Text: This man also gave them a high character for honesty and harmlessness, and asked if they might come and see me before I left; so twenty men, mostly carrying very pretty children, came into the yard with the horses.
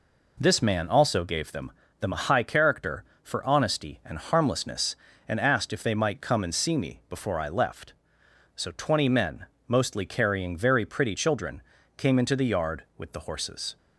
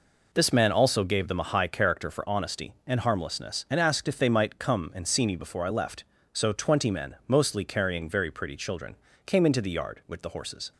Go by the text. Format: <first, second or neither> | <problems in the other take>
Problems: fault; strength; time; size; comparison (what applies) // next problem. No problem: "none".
second | says "them" twice; at 2.0 s